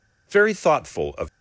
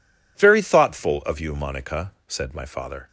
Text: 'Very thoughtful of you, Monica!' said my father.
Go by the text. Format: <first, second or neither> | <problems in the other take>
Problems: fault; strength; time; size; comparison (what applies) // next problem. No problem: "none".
second | stops before "you Monica said my father"; at 1.2 s